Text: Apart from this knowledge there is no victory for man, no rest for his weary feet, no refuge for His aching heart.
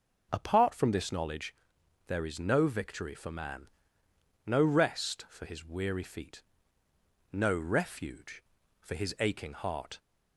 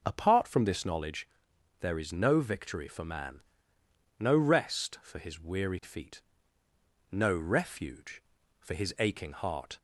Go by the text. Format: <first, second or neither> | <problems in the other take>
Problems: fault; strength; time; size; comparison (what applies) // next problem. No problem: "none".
neither | pauses between "knowledge" and "there"; noticeable; the same in both